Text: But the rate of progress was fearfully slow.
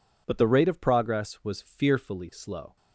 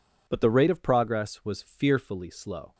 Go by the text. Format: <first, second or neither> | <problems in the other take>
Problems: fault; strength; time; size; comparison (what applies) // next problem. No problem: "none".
neither | none